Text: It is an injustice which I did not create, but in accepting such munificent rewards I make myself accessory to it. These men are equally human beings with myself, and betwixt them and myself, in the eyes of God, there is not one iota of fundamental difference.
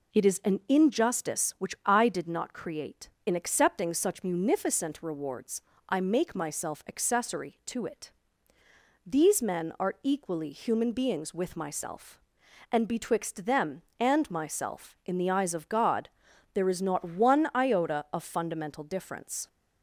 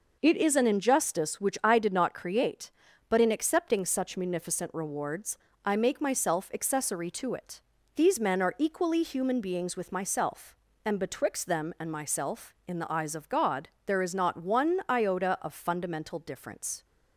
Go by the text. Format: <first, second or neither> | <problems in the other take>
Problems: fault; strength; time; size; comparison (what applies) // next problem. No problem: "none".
second | skips "but"; at 3.1 s // pauses between "rewards" and "I"; slight; at 5.6 s; 0.28 s long; slight in the second